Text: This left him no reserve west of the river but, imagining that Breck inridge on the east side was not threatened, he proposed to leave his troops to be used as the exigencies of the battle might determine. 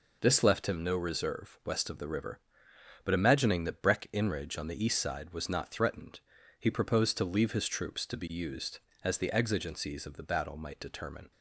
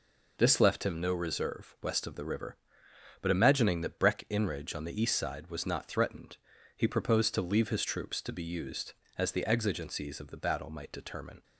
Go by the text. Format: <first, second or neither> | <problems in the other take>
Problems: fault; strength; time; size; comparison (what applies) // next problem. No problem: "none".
neither | none